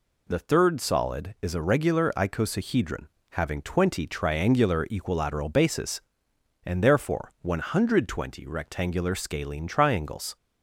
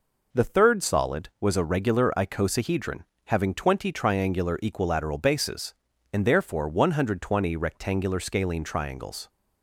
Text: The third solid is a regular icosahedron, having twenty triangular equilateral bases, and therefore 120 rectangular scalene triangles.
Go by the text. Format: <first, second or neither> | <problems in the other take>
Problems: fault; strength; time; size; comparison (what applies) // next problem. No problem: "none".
first | says "was" for "is"; at 1.4 s